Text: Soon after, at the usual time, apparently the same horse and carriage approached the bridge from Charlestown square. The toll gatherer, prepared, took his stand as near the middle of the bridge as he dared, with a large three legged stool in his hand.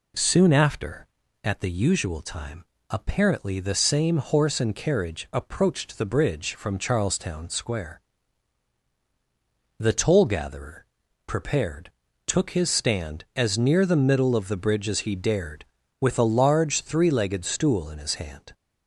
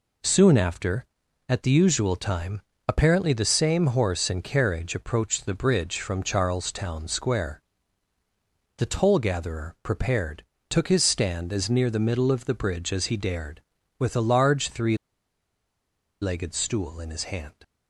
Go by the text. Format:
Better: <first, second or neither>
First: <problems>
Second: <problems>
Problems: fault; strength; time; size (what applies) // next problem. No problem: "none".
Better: first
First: none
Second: pauses between "three" and "legged"; strong; at 14.9 s; 1.2 s long